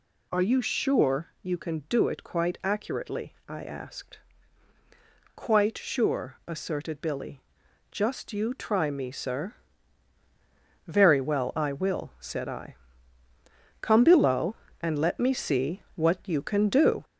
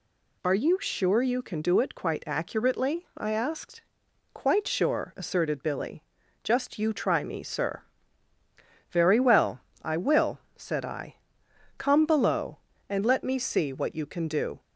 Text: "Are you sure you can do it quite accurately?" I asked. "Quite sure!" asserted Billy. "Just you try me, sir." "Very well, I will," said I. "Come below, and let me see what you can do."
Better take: second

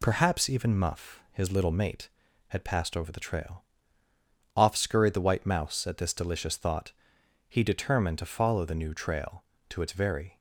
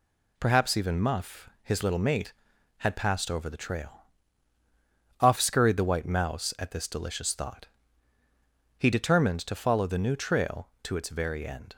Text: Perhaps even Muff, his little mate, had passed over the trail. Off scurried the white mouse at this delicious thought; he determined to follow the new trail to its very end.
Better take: second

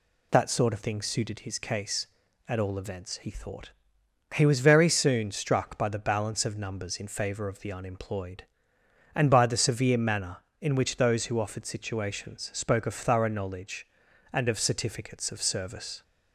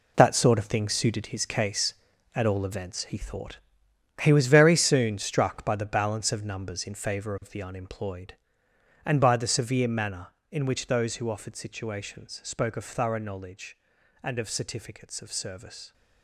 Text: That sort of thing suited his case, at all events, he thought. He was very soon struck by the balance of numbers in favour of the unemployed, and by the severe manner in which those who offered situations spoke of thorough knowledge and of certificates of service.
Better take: first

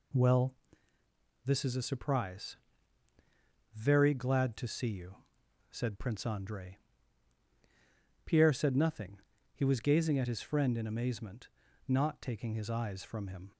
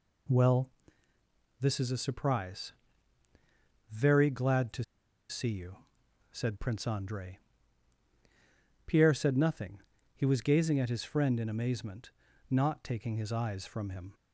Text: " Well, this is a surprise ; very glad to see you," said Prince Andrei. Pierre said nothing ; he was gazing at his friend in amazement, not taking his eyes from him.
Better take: first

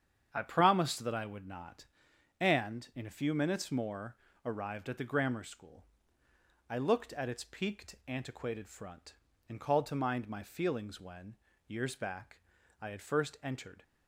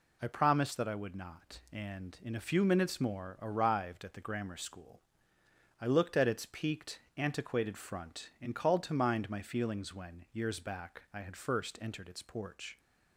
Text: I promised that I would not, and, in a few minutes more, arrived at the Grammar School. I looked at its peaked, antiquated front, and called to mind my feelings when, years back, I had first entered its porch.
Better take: second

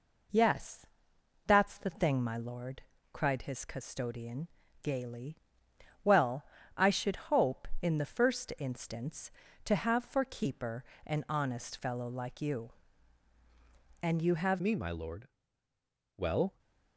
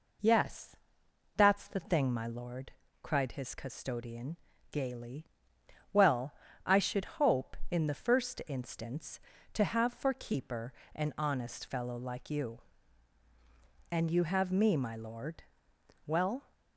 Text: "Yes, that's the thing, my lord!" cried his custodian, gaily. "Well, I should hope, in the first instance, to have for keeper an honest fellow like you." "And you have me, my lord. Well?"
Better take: second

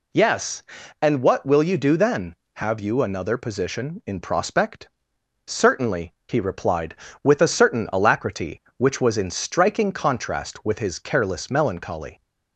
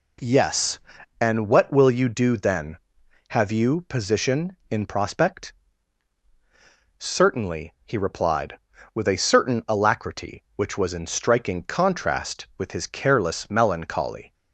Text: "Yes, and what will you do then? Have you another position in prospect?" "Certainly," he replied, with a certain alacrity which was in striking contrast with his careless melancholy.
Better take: first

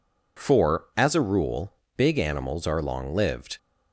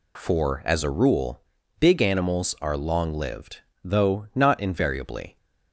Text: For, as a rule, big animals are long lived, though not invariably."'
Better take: second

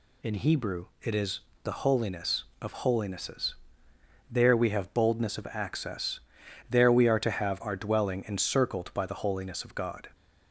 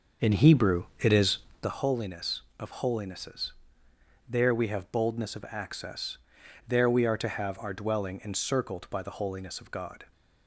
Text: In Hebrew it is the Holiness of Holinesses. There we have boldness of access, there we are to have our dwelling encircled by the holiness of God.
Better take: first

